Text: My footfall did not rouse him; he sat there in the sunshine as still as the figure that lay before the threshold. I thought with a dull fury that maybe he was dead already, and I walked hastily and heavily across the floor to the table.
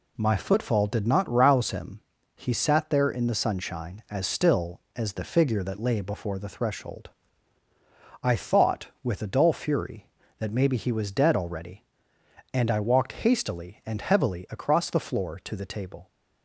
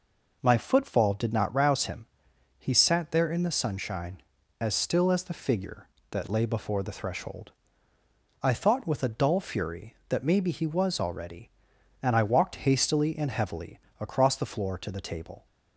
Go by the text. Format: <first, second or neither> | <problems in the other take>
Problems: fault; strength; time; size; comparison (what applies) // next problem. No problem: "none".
first | skips "dead"; at 10.9 s // pauses between "heavily" and "across"; slight; at 13.7 s; 0.20 s long